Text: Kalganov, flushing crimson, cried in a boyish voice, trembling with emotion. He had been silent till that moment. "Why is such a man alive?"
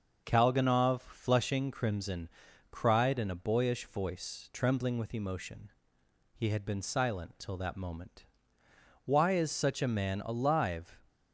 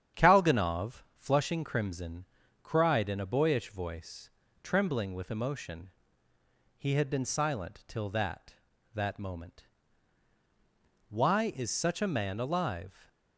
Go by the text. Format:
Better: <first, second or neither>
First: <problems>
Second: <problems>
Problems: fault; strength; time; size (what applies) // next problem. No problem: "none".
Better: first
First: starts louder than the rest; until 1.2 s; 6 dB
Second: starts louder than the rest; strong; until 1.2 s; 9 dB // says "that" twice; at 8.9 s